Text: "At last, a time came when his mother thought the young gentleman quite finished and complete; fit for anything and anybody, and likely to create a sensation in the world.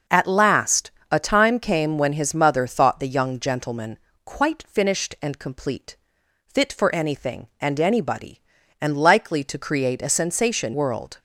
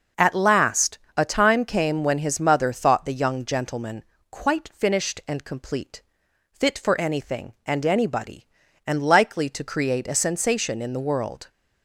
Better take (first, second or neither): second